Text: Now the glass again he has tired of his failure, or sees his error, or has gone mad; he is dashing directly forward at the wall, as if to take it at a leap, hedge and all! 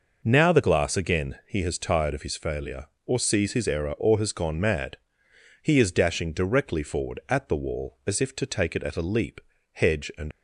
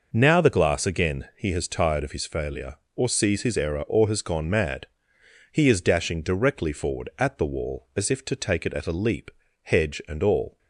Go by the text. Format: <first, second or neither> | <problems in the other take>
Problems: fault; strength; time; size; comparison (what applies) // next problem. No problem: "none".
second | stops before "all"; at 10.3 s